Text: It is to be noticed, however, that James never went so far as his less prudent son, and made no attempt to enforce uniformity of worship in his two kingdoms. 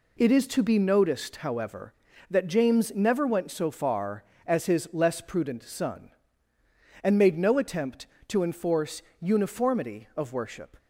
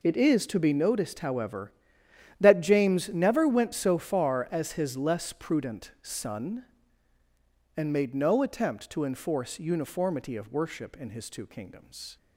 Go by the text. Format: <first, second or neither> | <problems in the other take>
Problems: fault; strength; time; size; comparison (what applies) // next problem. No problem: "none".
second | pauses between "enforce" and "uniformity"; slight; at 9.0 s; 0.18 s long // stops before "in his two kingdoms"; at 10.7 s